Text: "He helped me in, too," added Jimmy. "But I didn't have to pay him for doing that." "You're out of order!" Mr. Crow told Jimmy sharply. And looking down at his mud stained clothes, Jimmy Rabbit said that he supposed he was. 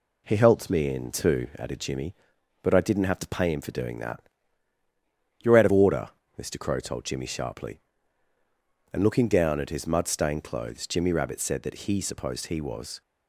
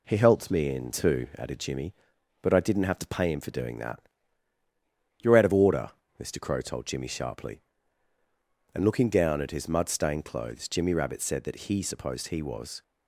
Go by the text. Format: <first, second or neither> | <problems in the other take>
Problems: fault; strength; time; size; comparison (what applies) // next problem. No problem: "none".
neither | none